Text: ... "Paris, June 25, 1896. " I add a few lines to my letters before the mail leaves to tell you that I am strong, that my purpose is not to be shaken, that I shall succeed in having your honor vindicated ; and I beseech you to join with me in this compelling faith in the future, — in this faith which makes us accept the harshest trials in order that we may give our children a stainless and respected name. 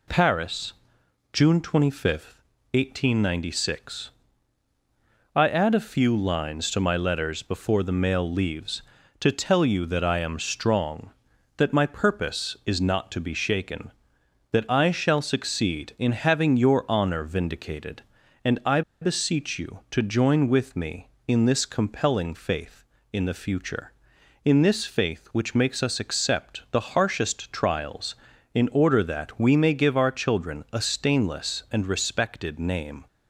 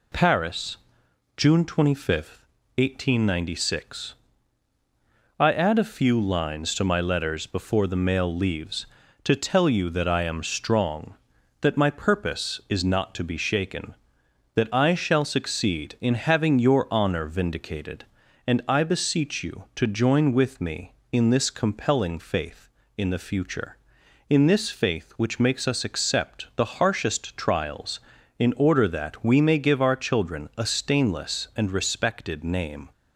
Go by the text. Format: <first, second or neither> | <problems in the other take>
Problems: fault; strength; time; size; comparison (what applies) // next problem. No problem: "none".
second | pauses between "I" and "beseech"; slight; at 18.8 s; 0.20 s long